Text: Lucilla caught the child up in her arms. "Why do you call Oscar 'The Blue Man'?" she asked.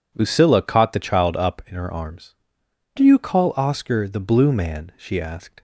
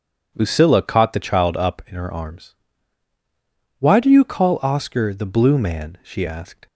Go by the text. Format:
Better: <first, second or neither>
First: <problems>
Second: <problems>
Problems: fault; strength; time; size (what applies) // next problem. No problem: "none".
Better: second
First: skips "Why"; at 2.6 s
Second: none